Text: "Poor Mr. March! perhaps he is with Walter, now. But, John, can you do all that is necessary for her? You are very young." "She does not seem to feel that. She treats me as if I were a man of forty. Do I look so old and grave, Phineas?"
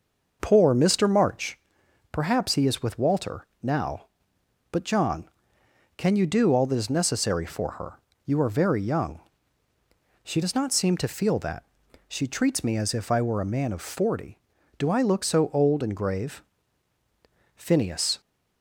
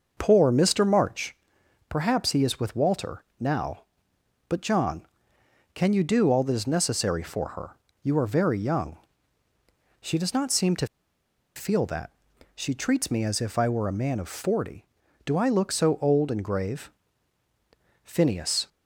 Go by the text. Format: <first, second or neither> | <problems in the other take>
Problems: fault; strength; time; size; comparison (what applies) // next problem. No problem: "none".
first | pauses between "to" and "feel"; noticeable; at 10.8 s; 0.68 s long